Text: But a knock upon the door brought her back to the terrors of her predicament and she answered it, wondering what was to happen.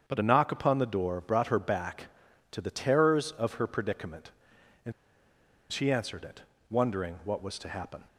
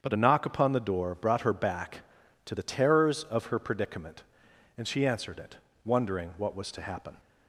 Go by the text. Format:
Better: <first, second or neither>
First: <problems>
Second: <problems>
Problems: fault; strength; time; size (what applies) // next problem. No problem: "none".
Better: second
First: starts louder than the rest; strong; until 1.0 s; 7.5 dB // pauses between "and" and "she"; noticeable; at 4.9 s; 0.79 s long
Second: starts louder than the rest; strong; until 1.0 s; 7.5 dB